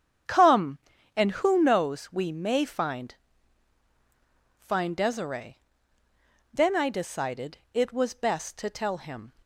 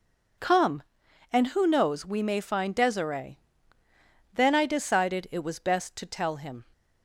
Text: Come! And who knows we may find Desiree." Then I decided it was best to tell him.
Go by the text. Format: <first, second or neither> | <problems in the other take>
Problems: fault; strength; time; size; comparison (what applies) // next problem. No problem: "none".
second | starts louder than the rest; strong; until 1.6 s; 8.5 dB // says "find" twice; at 4.5 s